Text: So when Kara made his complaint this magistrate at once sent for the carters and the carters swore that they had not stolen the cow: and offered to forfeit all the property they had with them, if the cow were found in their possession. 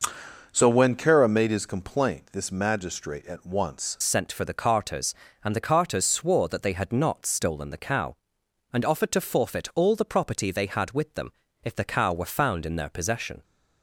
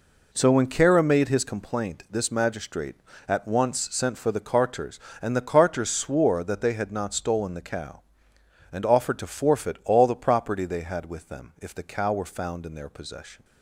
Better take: second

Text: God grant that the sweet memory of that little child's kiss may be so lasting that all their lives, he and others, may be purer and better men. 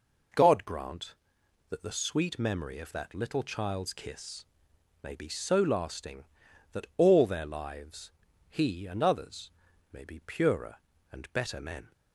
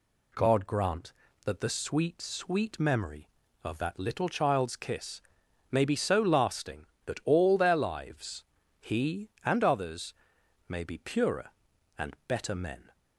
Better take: first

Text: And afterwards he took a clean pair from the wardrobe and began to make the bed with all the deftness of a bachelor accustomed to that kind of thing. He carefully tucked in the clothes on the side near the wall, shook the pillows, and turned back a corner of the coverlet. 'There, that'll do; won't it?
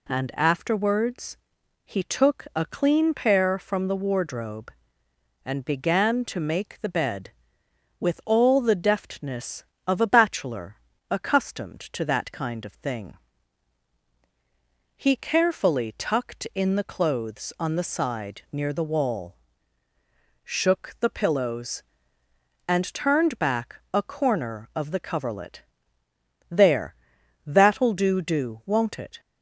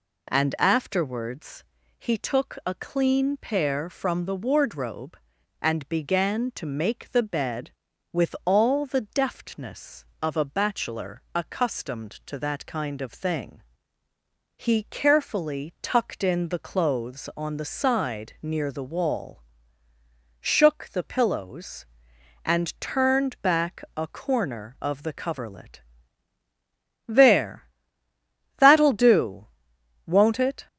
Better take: second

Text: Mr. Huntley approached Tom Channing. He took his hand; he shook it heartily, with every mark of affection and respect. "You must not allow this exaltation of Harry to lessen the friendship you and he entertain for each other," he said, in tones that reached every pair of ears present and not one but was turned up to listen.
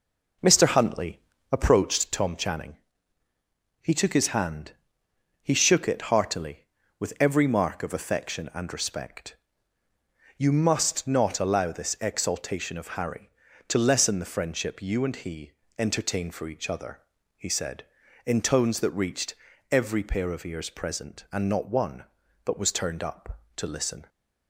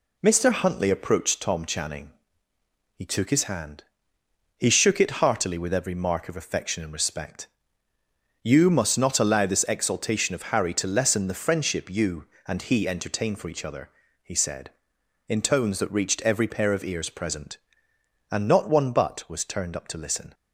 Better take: second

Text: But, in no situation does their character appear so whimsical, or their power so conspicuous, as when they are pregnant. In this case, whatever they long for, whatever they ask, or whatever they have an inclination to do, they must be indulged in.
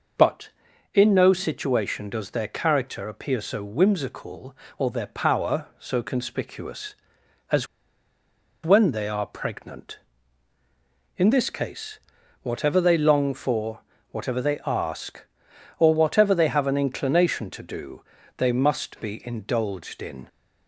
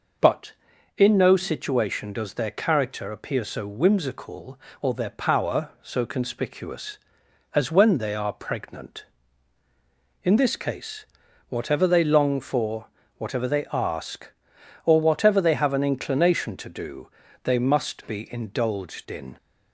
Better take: second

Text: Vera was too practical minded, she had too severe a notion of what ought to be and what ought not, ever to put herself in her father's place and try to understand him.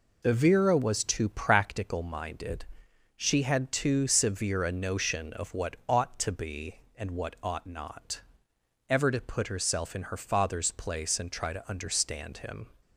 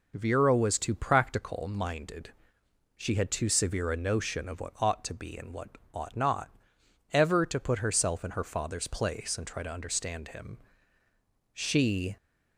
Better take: first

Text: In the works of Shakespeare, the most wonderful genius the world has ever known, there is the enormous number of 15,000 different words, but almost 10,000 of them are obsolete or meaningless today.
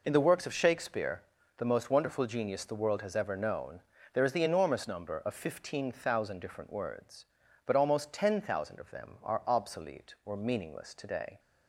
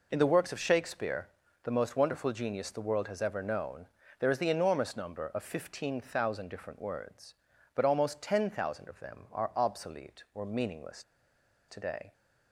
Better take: first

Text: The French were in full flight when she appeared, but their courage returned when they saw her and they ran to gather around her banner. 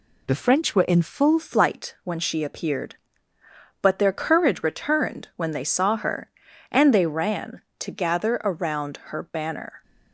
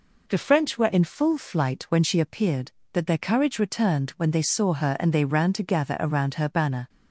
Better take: second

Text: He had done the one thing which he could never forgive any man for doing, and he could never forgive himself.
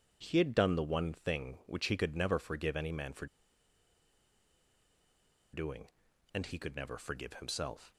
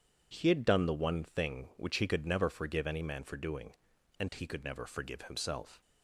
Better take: second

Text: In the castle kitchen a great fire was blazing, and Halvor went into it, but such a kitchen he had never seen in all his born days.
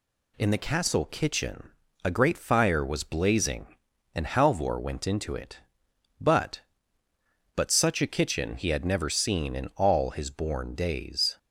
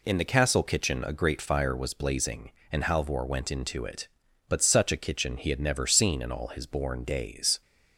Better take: second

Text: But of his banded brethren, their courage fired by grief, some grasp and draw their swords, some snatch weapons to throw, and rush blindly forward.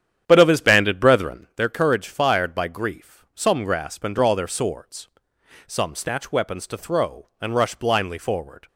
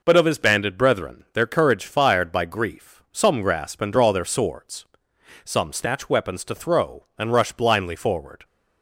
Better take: second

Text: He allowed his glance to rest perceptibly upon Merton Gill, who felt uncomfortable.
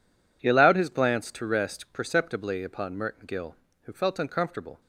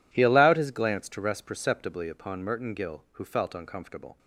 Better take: neither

